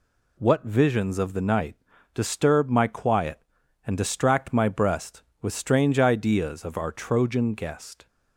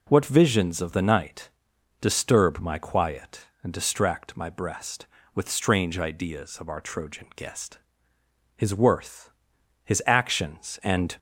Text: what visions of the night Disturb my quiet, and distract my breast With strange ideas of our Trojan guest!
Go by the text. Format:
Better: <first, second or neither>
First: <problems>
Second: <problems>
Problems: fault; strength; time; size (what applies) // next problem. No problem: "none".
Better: first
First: pauses between "night" and "Disturb"; at 1.7 s; 0.38 s long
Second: pauses between "night" and "Disturb"; noticeable; at 1.4 s; 0.50 s long // goes on to say "His worth his actions and"; strong; from 8.5 s on; 2.6 s long